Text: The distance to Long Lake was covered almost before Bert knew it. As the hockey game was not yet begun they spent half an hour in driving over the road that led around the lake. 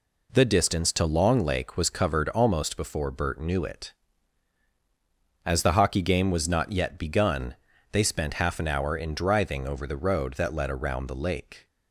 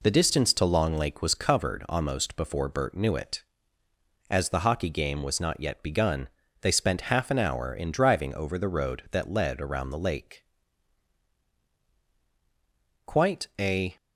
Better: first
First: pauses between "begun" and "they"; at 7.5 s; 0.38 s long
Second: pauses between "begun" and "they"; slight; at 6.2 s; 0.34 s long // goes on to say "Quite a"; noticeable; from 13.0 s on; 0.92 s long

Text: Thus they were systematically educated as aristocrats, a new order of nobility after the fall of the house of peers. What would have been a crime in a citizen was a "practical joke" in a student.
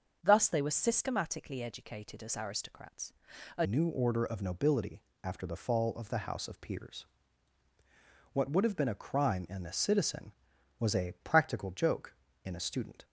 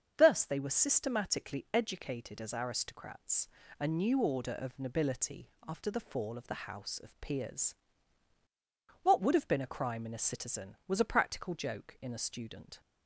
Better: second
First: starts louder than the rest; until 1.2 s; 6.5 dB // changes voice at "new"; from 3.6 s on; 9.4 s long // pauses between "nobility" and "after"; slight; at 5.0 s; 0.20 s long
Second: starts louder than the rest; until 1.1 s; 7 dB // pauses between "nobility" and "after"; slight; at 5.4 s; 0.18 s long

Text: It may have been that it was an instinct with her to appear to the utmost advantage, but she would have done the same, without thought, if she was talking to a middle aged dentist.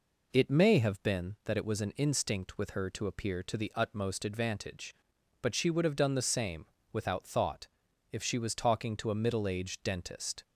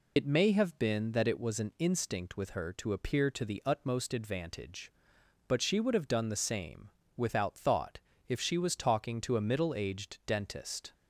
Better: first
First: none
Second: loses the start of "It"; at 0.1 s; 65 ms

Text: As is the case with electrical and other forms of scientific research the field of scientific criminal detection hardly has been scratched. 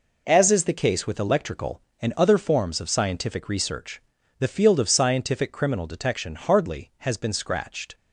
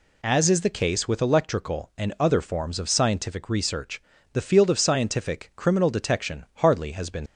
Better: first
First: pauses between "research" and "the"; at 4.0 s; 0.38 s long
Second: pauses between "research" and "the"; slight; at 4.0 s; 0.32 s long // stops before "scratched"; at 7.2 s

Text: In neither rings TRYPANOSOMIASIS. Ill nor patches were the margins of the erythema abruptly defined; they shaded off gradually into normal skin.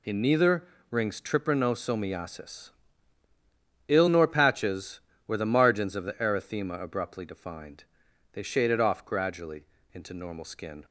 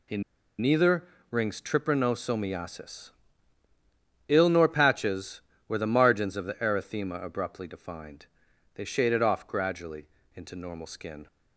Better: first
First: pauses between "neither" and "rings"; slight; at 0.6 s; 0.24 s long // pauses between "gradually" and "into"; slight; at 9.6 s; 0.28 s long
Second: pauses between "In" and "neither"; at 0.2 s; 0.37 s long // pauses between "neither" and "rings"; slight; at 1.0 s; 0.24 s long // pauses between "gradually" and "into"; slight; at 10.0 s; 0.28 s long

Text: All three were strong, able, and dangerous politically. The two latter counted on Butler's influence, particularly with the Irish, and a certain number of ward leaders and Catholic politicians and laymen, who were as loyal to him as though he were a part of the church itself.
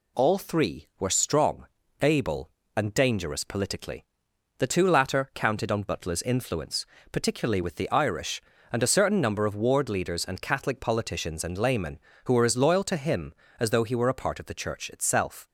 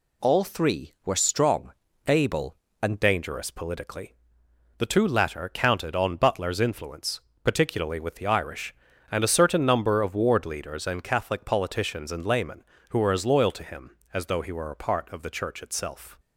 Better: first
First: none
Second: changes voice at "dangerous"; from 2.9 s on; 13.2 s long

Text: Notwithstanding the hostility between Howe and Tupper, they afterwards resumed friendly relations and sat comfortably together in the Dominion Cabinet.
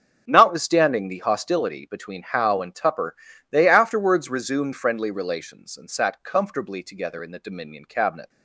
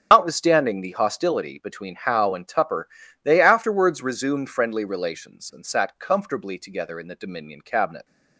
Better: first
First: starts louder than the rest; until 1.2 s; 7 dB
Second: loses the start of "Notwithstanding"; at 0.1 s; 110 ms // starts louder than the rest; strong; until 1.1 s; 9 dB

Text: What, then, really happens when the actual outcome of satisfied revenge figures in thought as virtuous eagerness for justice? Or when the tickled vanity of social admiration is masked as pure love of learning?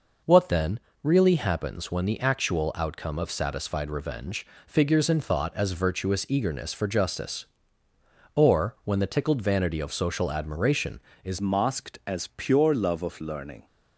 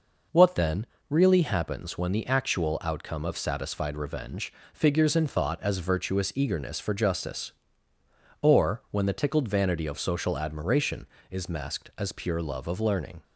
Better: second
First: pauses between "revenge" and "figures"; slight; at 4.4 s; 0.20 s long // changes voice at "masked"; from 11.4 s on; 2.2 s long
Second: pauses between "revenge" and "figures"; slight; at 4.5 s; 0.20 s long

